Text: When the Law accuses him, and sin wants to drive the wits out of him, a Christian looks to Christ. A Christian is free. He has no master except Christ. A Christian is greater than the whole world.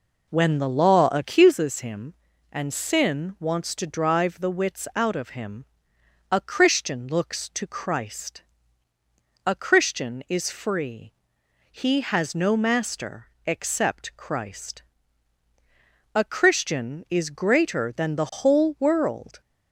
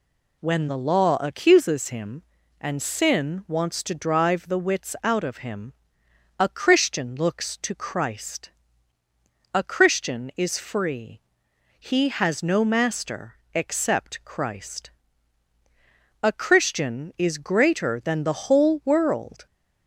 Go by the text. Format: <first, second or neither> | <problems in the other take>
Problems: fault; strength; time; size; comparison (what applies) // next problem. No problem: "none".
second | starts louder than the rest; noticeable; until 1.5 s; 4 dB // pauses between "master" and "except"; slight; at 13.2 s; 0.18 s long; slight in the second